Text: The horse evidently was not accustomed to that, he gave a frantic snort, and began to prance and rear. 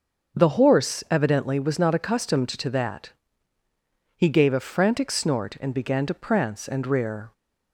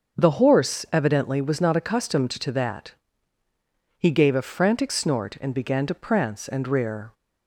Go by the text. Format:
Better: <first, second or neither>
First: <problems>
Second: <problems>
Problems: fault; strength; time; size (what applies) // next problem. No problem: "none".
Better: neither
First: starts louder than the rest; until 1.4 s; 6.5 dB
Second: starts louder than the rest; until 1.2 s; 6.5 dB